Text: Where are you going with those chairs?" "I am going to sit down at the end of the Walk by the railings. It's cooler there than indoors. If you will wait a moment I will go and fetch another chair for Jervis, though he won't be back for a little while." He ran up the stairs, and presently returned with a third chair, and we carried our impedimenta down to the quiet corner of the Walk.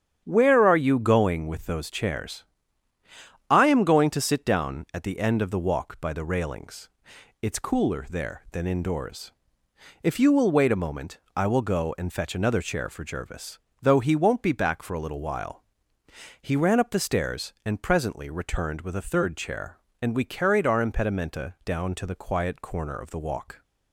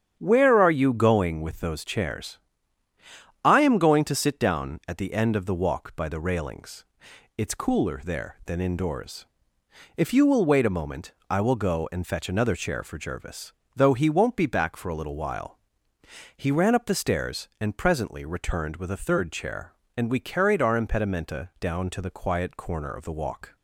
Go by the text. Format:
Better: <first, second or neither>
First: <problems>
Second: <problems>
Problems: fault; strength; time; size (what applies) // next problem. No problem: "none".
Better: neither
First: starts louder than the rest; strong; until 1.2 s; 8 dB // pauses between "moment" and "I"; slight; at 11.1 s; 0.18 s long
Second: starts louder than the rest; strong; until 1.2 s; 8 dB // pauses between "moment" and "I"; slight; at 11.1 s; 0.18 s long